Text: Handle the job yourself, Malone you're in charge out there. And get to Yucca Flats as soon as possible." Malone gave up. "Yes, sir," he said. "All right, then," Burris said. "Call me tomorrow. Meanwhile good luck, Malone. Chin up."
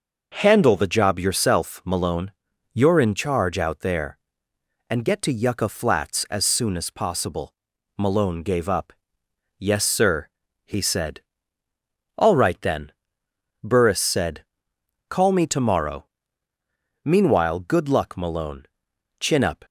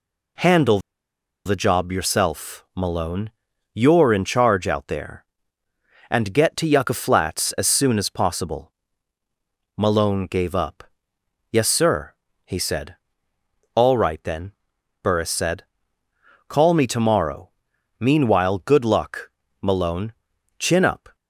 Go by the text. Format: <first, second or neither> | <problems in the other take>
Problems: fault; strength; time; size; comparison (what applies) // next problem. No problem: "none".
first | pauses between "Handle" and "the"; noticeable; at 0.7 s; 0.67 s long // pauses between "Malone" and "you're"; at 3.3 s; 0.42 s long; also in the first